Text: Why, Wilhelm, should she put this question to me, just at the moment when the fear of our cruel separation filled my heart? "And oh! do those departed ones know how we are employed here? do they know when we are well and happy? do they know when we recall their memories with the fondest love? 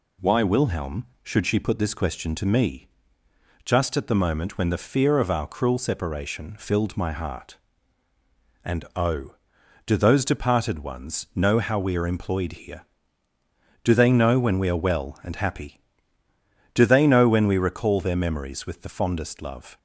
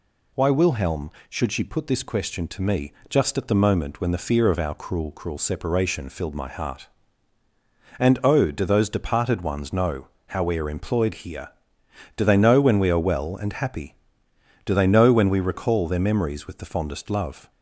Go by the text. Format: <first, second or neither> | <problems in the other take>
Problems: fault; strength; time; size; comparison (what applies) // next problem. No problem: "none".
first | says "cruel" twice; at 5.1 s // pauses between "know" and "how"; slight; at 10.0 s; 0.20 s long